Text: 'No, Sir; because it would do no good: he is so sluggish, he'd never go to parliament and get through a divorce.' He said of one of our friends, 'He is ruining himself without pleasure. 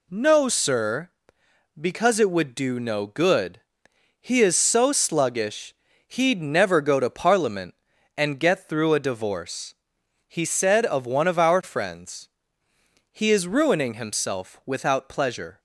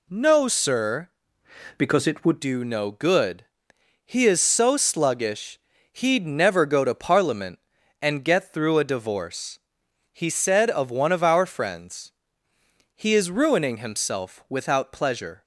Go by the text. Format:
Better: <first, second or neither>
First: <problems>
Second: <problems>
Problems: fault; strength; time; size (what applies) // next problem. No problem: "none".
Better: first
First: none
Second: changes voice from "because" to "would"; from 1.7 to 2.4 s; 0.7 s long